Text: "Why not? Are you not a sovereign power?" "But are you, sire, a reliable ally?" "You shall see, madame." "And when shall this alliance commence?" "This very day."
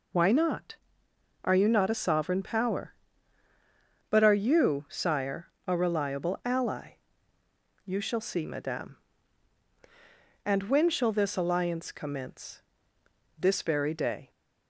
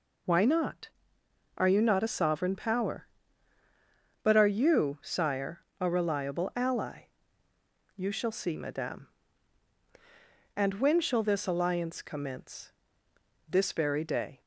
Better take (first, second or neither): neither